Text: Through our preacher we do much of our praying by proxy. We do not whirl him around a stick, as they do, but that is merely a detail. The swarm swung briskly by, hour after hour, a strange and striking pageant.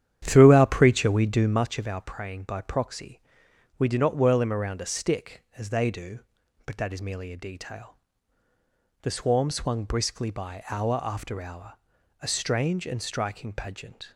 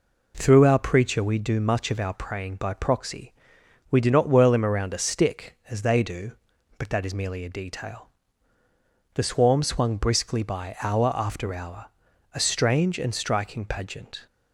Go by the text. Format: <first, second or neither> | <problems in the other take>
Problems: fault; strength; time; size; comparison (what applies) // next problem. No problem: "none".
second | starts louder than the rest; strong; until 1.7 s; 10 dB